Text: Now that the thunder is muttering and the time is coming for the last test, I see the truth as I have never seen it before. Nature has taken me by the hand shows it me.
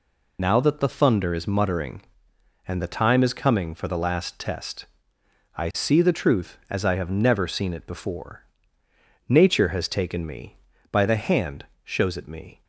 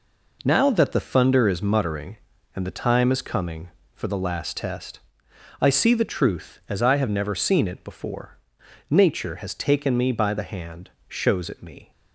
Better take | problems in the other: second | loses the start of "Now"; at 0.3 s; 35 ms // pauses between "hand" and "shows"; slight; at 11.6 s; 0.20 s long; slight in the second

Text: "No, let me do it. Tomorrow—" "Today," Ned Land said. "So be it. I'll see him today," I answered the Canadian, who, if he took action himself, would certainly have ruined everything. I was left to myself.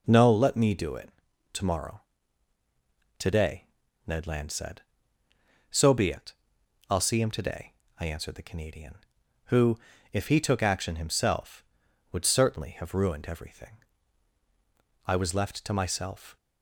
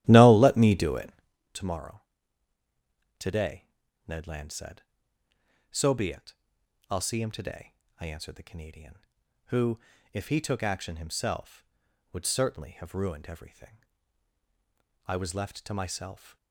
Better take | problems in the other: first | starts louder than the rest; strong; until 1.4 s; 14 dB

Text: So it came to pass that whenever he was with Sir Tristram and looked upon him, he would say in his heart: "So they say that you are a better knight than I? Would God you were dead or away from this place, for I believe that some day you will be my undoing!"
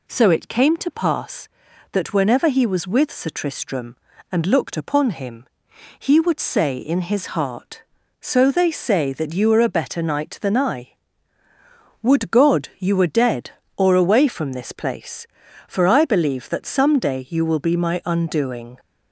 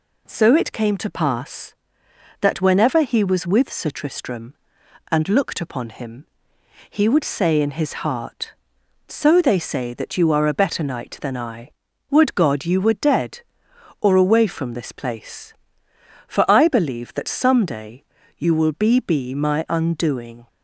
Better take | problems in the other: first | pauses between "day" and "you"; slight; at 18.0 s; 0.36 s long // says "be" twice; at 18.9 s

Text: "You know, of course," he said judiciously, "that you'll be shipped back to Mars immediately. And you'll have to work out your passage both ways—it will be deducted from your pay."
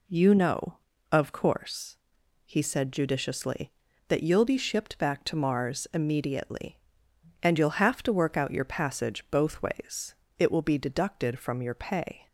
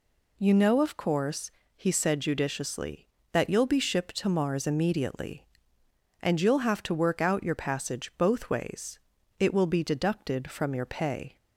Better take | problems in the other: first | skips "back"; at 4.1 s

